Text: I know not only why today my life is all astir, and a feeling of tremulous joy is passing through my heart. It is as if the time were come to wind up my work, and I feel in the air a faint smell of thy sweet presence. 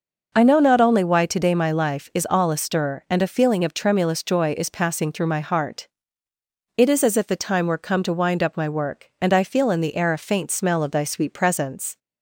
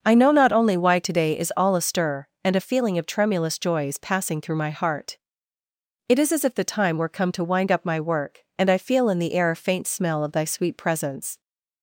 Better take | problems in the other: first | starts louder than the rest; until 1.0 s; 6.5 dB // skips "my life"; at 1.3 s

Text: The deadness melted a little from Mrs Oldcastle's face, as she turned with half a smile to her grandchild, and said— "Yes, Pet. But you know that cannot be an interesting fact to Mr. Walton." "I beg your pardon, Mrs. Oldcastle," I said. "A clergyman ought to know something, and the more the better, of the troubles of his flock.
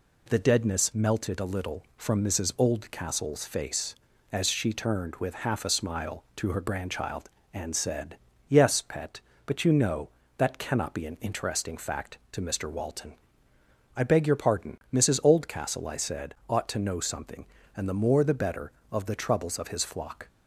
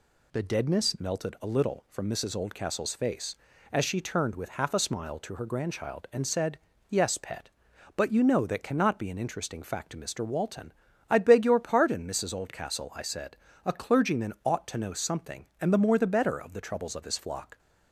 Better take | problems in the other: second | skips "A clergyman"; at 16.4 s

